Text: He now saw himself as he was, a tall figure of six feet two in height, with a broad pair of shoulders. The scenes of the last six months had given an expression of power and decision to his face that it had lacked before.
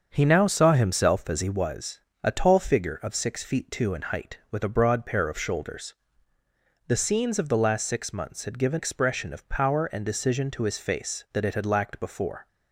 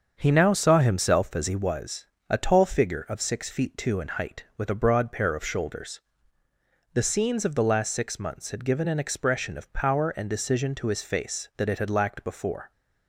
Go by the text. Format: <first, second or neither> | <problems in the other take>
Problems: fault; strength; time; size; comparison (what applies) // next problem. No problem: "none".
second | starts louder than the rest; until 1.1 s; 7 dB; also in the second // skips "an"; at 8.7 s